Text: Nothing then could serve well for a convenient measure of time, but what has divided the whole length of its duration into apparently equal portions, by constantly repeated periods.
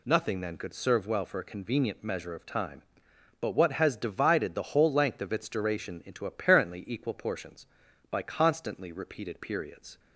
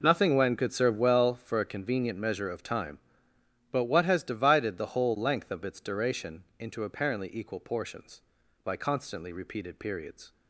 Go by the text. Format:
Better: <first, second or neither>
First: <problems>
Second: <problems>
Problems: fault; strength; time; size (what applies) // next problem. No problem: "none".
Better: first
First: none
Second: says "when" for "then"; at 0.3 s // pauses between "duration" and "into"; slight; at 6.4 s; 0.16 s long